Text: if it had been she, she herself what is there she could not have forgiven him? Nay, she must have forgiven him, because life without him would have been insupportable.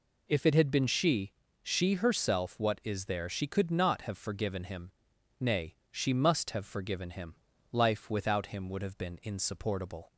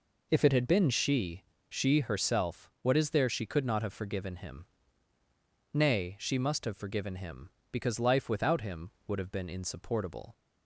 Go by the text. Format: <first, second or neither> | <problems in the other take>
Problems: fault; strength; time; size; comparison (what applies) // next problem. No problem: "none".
second | skips "because"; at 7.5 s